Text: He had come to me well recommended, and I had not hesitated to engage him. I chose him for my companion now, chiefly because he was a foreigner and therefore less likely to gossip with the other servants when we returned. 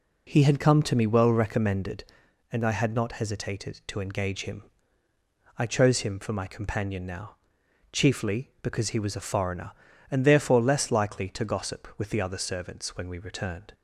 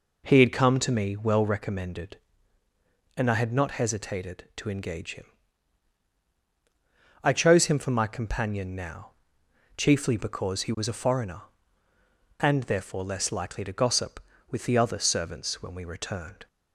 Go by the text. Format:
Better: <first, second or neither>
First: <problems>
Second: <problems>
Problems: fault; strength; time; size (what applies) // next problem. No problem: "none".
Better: neither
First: none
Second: none